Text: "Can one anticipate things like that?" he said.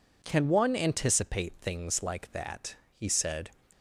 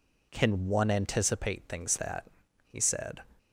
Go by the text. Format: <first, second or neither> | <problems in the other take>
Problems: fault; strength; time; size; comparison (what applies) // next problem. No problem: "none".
first | skips "like"; at 1.9 s